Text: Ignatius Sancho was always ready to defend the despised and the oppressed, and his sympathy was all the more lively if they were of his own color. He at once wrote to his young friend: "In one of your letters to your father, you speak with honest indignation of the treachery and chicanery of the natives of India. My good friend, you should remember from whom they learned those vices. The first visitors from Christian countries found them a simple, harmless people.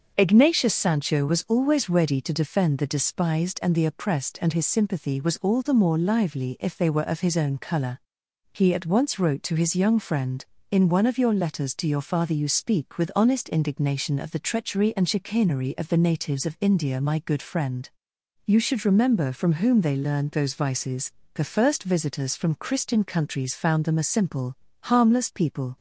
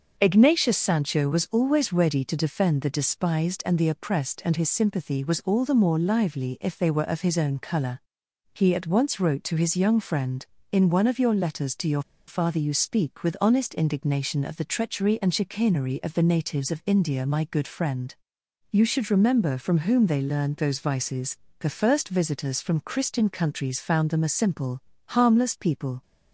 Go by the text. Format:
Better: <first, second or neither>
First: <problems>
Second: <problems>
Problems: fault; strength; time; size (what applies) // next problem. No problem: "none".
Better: first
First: starts louder than the rest; until 1.1 s; 6.5 dB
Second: starts louder than the rest; until 1.1 s; 6.5 dB // pauses between "your" and "father"; slight; at 12.0 s; 0.26 s long